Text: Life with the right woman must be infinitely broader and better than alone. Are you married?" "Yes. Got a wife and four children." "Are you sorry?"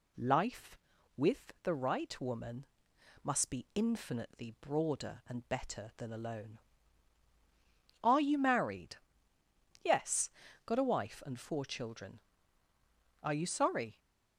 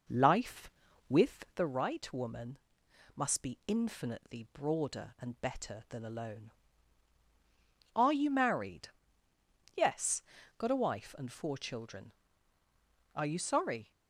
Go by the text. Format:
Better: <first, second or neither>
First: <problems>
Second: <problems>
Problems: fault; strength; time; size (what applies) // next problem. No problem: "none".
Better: first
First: pauses between "woman" and "must"; noticeable; at 2.6 s; 0.58 s long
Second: starts louder than the rest; noticeable; until 1.7 s; 5 dB // pauses between "woman" and "must"; noticeable; at 2.5 s; 0.58 s long